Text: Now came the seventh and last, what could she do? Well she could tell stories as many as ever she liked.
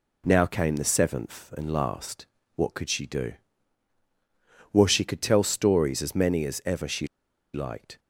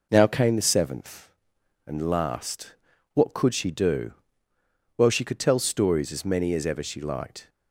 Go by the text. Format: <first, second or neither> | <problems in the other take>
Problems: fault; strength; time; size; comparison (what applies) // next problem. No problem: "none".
second | pauses between "she" and "liked"; noticeable; at 7.0 s; 0.48 s long